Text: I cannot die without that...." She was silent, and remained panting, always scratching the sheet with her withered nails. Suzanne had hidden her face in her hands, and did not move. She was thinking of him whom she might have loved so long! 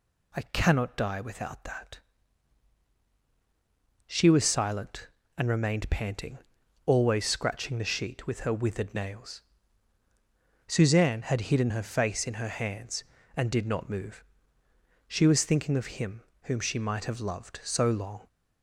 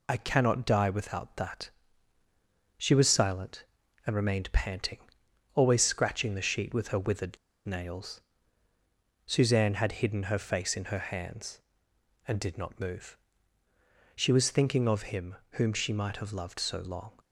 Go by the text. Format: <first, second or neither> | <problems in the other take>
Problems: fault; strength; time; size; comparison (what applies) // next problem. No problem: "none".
first | pauses between "withered" and "nails"; slight; at 7.3 s; 0.28 s long // pauses between "him" and "whom"; slight; at 15.3 s; 0.16 s long; slight in the first